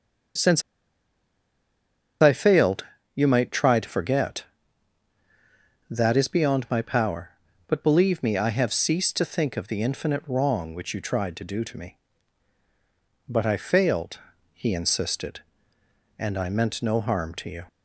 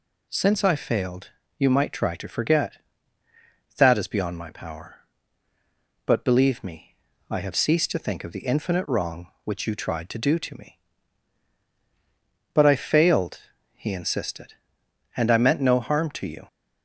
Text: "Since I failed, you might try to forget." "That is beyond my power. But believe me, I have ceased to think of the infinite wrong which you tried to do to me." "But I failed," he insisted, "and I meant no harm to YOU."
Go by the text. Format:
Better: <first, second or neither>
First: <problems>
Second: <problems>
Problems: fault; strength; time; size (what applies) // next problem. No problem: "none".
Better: second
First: starts louder than the rest; until 3.2 s; 7 dB // pauses between "Since" and "I"; strong; at 0.6 s; 1.5 s long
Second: none